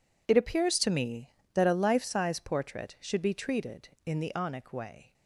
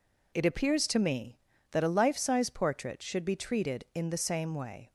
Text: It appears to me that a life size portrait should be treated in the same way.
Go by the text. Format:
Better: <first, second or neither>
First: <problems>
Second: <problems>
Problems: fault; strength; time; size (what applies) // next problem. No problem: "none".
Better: second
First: says "onic" for "same"; at 4.3 s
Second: none